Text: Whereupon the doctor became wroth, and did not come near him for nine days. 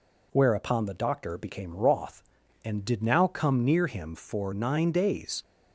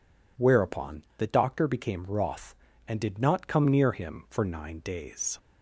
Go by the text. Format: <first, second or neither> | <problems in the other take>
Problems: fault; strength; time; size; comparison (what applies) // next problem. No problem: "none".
second | says "now" for "not"; at 3.0 s